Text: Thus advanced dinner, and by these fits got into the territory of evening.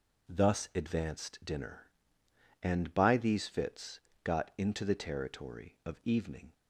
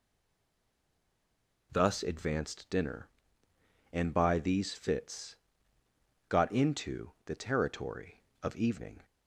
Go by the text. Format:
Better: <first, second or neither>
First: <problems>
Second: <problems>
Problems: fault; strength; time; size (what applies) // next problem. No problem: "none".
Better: first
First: pauses between "fits" and "got"; slight; at 3.9 s; 0.24 s long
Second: stays silent before the first word; noticeable; until 1.7 s; 1.7 s long // pauses between "fits" and "got"; noticeable; at 5.3 s; 0.92 s long